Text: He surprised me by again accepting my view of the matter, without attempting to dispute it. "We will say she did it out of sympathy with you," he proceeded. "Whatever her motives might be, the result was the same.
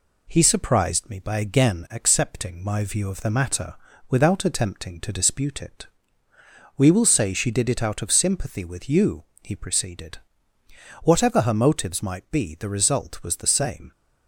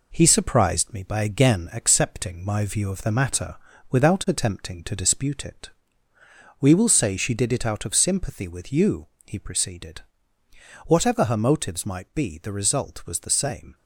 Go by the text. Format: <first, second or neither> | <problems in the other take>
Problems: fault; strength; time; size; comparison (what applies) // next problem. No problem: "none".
first | gets quieter; noticeable; throughout; 4.5 dB